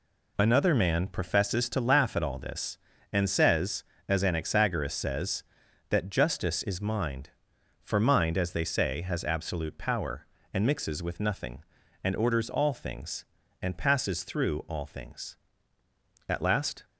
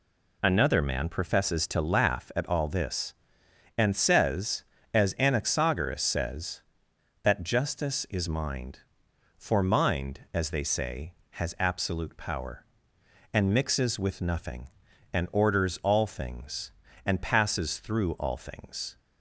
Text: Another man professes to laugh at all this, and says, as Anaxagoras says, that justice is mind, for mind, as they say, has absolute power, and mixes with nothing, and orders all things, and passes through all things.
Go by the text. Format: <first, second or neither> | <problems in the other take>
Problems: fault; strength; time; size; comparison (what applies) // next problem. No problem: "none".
second | goes on to say "At last"; from 16.2 s on; 0.56 s long